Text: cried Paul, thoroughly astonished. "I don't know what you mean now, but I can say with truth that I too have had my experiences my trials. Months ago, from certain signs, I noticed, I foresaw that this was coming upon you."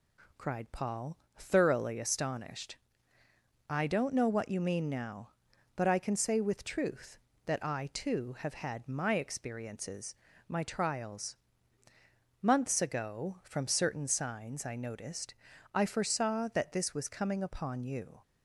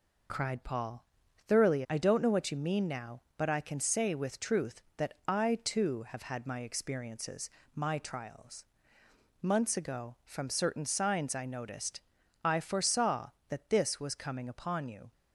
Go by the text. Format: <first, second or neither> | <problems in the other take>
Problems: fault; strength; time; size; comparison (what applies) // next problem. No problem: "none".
first | skips "astonished"; at 1.8 s // pauses between "experiences" and "my"; slight; at 7.4 s; 0.28 s long; slight in the first